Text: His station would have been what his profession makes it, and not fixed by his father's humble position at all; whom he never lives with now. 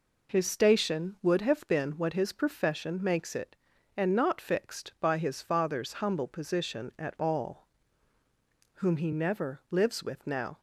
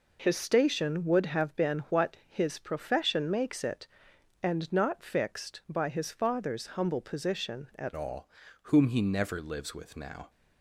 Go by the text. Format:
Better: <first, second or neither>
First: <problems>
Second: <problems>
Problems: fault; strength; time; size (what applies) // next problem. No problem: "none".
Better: first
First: none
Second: changes voice at "all"; from 7.9 s on; 2.3 s long